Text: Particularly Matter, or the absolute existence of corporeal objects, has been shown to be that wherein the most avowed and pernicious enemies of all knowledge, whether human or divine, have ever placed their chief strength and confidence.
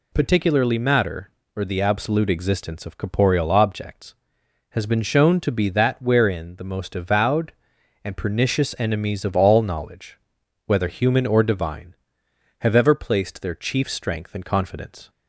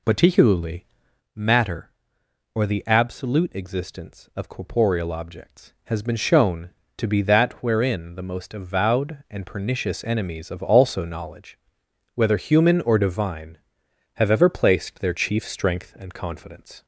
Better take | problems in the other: first | pauses between "Particularly" and "Matter"; noticeable; at 0.8 s; 0.50 s long // says "also" for "all"; at 10.6 s

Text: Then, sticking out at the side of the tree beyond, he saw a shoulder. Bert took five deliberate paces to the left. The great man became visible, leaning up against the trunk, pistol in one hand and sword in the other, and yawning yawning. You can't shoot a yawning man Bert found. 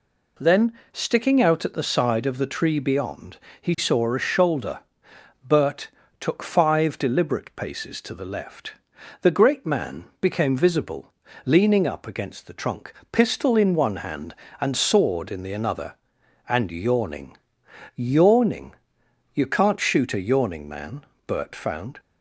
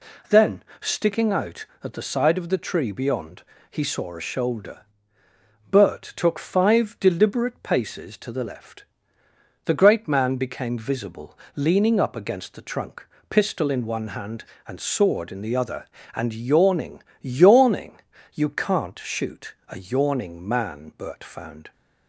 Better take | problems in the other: second | pauses between "Bert" and "took"; slight; at 5.8 s; 0.32 s long // pauses between "man" and "became"; slight; at 10.0 s; 0.16 s long // says "another" for "other"; at 15.5 s // pauses between "yawning" and "yawning"; noticeable; at 17.3 s; 0.60 s long; slight in the second // pauses between "man" and "Bert"; slight; at 21.0 s; 0.24 s long

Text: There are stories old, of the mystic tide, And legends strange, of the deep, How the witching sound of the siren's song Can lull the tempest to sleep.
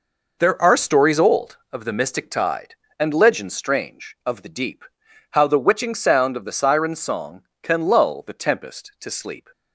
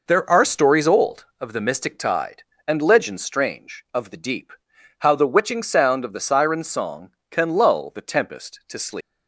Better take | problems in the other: first | leaves "sleep" unfinished; at 9.0 s; 180 ms

